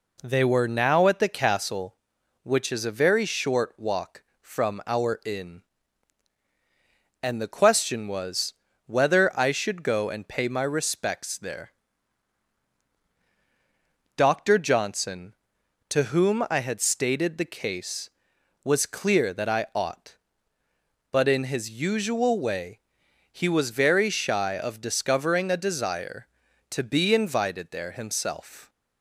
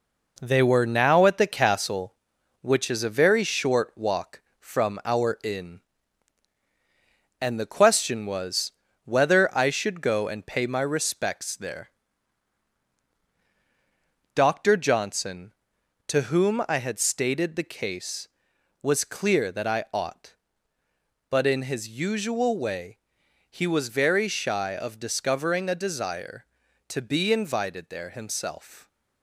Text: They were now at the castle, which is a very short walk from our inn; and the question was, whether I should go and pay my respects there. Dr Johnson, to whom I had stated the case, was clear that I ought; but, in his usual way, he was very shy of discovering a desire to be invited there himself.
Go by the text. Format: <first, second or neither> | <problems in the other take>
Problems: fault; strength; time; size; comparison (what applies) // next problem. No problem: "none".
first | gets quieter; noticeable; throughout; 5 dB